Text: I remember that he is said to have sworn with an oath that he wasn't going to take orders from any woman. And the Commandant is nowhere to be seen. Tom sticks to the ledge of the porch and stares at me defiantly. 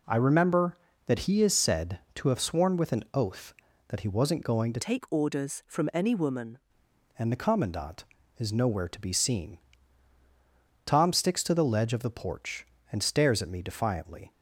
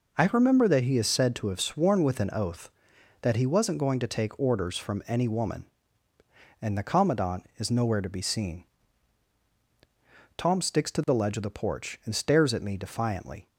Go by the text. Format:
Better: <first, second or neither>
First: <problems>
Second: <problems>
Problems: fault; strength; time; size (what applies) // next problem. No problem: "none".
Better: second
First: changes voice from "take" to "woman"; from 4.8 to 6.5 s; 1.7 s long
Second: none